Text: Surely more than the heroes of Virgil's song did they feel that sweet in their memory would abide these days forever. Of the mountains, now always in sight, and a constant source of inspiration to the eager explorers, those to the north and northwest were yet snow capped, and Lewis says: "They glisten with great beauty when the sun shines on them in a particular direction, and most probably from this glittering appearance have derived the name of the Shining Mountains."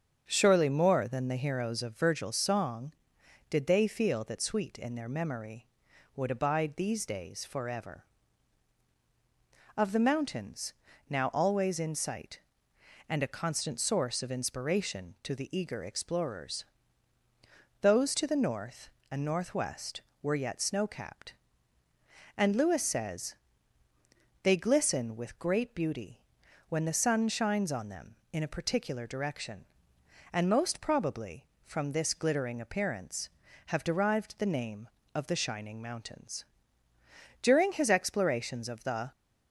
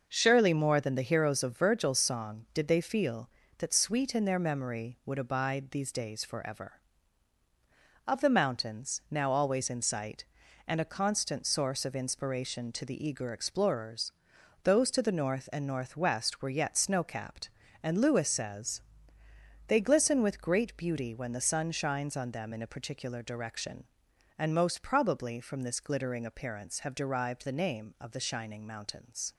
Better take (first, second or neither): second